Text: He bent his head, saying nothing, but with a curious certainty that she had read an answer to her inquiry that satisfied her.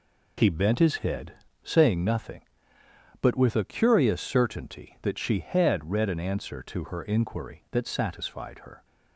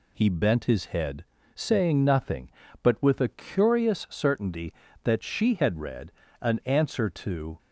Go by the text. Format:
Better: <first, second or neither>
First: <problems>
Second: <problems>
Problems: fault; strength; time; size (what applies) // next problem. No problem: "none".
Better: first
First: none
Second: pauses between "read" and "an"; slight; at 6.0 s; 0.30 s long // stops before "her inquiry that satisfied her"; at 7.5 s